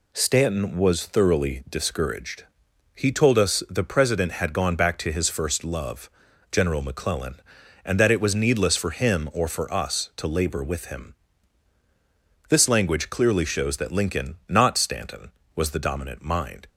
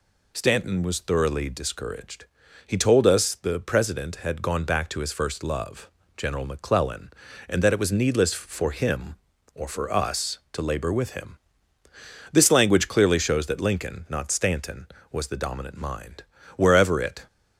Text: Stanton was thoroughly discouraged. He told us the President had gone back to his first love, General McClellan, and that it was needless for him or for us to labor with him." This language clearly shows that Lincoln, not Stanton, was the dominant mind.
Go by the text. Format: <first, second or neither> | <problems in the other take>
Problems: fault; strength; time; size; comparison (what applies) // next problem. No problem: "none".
first | goes on to say "Wherever it"; noticeable; from 16.5 s on; 0.70 s long